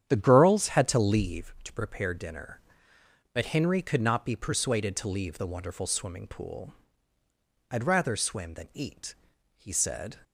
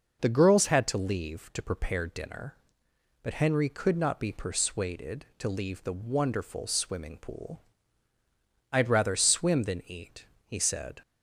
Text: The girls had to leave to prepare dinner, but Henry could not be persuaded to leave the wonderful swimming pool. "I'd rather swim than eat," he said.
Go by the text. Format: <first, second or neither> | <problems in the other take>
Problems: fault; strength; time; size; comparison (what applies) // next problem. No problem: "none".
second | starts louder than the rest; strong; until 1.5 s; 9 dB